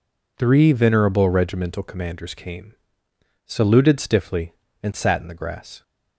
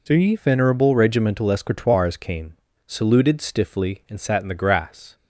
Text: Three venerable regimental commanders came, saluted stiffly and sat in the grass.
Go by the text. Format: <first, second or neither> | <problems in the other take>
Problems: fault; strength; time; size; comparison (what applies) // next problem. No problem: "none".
first | says "escritoires" for "commanders"; at 1.4 s